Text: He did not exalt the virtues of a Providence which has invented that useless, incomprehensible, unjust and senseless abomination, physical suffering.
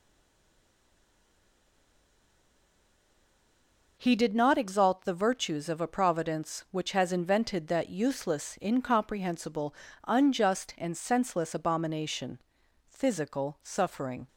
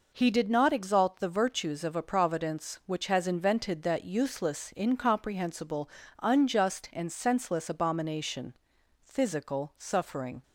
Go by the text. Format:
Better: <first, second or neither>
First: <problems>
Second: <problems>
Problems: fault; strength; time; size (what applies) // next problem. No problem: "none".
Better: second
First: stays silent before the first word; strong; until 3.9 s; 3.9 s long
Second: none